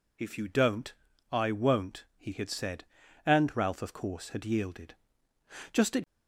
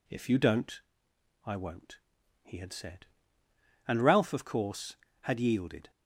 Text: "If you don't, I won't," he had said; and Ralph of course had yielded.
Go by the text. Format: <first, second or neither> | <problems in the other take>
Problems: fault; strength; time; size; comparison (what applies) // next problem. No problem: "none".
second | goes on to say "Just at"; slight; from 5.7 s on; 0.32 s long